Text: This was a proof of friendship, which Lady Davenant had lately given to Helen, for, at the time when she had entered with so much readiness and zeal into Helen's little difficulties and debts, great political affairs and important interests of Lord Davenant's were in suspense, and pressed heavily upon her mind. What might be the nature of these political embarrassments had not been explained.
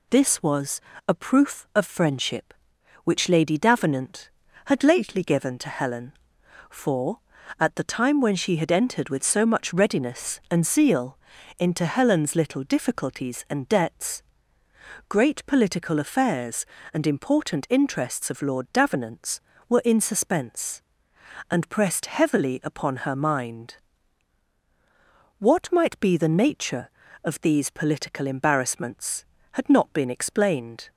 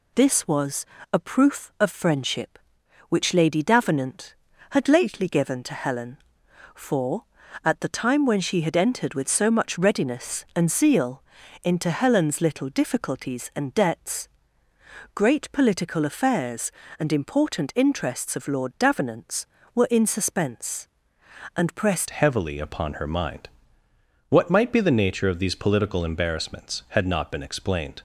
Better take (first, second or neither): first